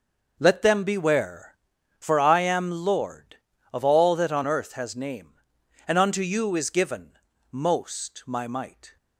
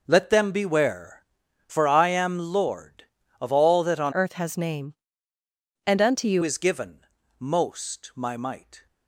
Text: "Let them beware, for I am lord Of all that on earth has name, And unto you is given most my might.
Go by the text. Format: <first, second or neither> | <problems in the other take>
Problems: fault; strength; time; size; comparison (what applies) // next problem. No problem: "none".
first | changes voice from "earth" to "you"; from 4.1 to 6.4 s; 2.3 s long // pauses between "given" and "most"; slight; at 7.0 s; 0.34 s long; slight in the first